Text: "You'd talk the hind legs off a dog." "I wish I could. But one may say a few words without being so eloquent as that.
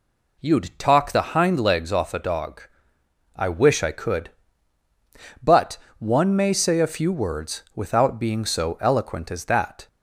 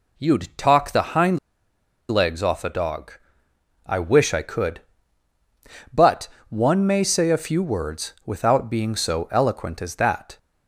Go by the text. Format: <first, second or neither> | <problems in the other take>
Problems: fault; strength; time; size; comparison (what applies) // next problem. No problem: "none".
first | pauses between "hind" and "legs"; noticeable; at 1.3 s; 0.72 s long // pauses between "But" and "one"; slight; at 6.2 s; 0.20 s long; slight in the first